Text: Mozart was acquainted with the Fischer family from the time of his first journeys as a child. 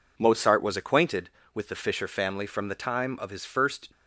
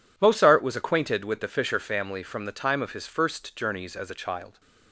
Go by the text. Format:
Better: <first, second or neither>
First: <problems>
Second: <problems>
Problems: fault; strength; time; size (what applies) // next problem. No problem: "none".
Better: second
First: stops before "journeys as a child"; at 3.9 s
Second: none